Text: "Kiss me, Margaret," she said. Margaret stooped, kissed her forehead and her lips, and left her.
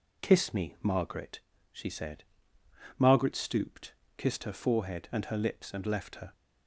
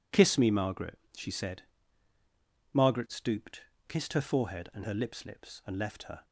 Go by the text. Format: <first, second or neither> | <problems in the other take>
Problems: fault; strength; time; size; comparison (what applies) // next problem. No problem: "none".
first | says "lips" twice; at 5.2 s